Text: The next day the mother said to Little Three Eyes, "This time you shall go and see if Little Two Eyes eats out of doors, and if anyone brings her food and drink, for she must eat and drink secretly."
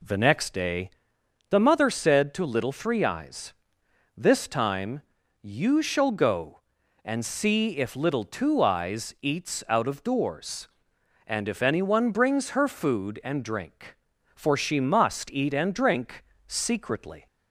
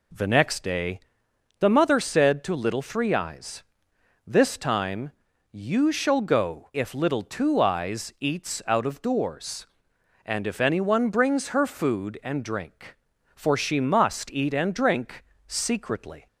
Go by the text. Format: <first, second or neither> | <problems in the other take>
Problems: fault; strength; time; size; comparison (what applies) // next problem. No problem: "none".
first | pauses between "day" and "the"; noticeable; at 0.9 s; 0.60 s long; noticeable in the first // pauses between "time" and "you"; at 5.1 s; 0.40 s long; also in the first // skips "and see"; at 6.7 s // pauses between "drink" and "secretly"; slight; at 15.2 s; 0.22 s long; slight in the first